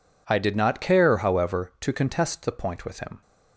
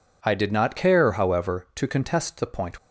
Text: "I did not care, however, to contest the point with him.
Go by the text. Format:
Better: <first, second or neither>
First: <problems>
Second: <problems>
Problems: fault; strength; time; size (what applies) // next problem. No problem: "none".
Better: first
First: none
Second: stops before "with him"; at 2.7 s